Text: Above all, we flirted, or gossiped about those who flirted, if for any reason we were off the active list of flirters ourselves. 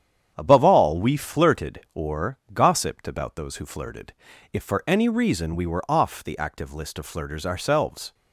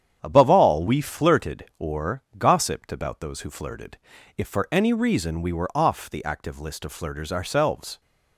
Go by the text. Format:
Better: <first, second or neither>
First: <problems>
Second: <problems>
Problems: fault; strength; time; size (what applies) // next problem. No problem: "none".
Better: neither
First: starts louder than the rest; strong; until 1.3 s; 9 dB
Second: starts louder than the rest; strong; until 1.2 s; 9 dB